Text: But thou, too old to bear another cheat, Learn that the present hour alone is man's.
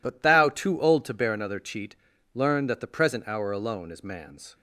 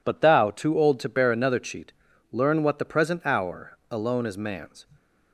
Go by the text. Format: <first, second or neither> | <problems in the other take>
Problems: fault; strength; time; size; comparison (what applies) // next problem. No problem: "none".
first | says "what" for "that"; at 2.6 s